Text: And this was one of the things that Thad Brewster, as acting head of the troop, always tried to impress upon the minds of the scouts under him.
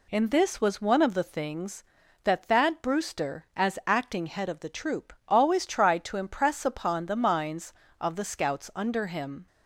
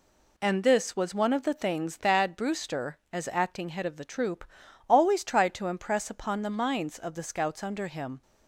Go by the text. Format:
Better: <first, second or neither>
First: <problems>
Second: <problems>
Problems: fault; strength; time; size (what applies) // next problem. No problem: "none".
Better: first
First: none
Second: skips "that"; at 1.9 s